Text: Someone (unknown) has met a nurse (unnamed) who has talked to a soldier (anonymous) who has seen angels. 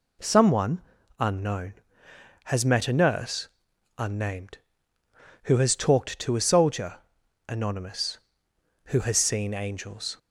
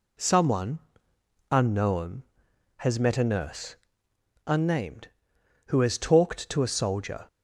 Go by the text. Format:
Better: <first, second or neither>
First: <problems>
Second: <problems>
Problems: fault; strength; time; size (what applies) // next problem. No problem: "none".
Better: first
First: none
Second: stops before "anonymous who has seen angels"; at 7.2 s